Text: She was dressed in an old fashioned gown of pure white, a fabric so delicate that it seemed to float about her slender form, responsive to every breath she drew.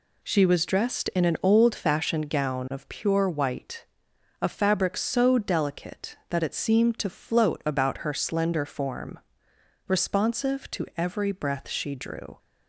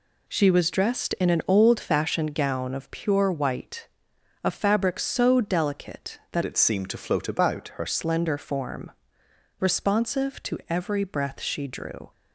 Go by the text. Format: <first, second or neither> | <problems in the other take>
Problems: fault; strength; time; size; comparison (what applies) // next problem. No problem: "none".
first | changes voice from "it" to "her"; from 6.4 to 7.8 s; 1.4 s long